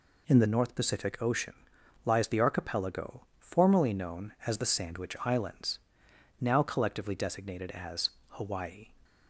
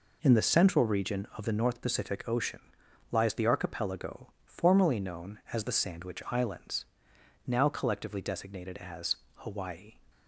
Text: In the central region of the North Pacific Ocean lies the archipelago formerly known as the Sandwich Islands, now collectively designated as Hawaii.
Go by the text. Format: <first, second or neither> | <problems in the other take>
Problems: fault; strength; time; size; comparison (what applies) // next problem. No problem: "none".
second | skips "central region of the"; at 0.4 s // pauses between "Ocean" and "lies"; noticeable; at 1.5 s; 0.52 s long; noticeable in the second // pauses between "as" and "Hawaii"; slight; at 8.0 s; 0.22 s long; slight in the second